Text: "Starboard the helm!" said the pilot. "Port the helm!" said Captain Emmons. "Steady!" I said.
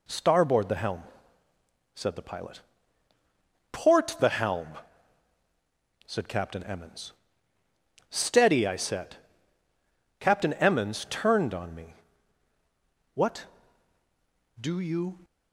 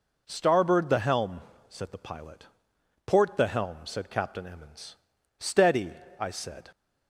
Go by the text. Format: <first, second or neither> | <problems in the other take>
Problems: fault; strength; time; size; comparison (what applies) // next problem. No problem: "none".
second | goes on to say "Captain Emmons turned on me What do you"; strong; from 10.2 s on; 4.9 s long